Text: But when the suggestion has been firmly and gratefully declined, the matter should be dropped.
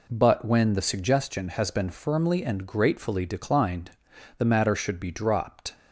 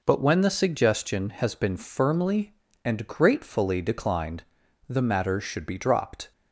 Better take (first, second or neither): neither